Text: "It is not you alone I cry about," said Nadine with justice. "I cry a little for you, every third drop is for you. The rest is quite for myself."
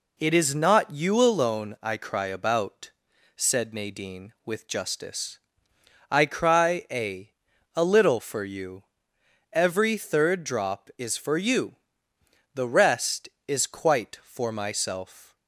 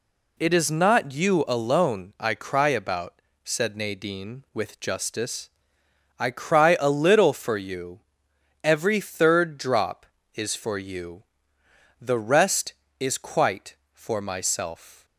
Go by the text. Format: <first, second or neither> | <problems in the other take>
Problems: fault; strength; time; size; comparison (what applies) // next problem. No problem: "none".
second | says "a" twice; at 7.7 s